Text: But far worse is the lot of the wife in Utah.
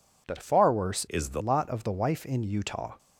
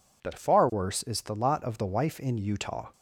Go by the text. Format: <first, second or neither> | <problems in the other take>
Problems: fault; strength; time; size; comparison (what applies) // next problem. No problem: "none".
second | changes voice from "is" to "the"; from 1.0 to 1.4 s; 0.4 s long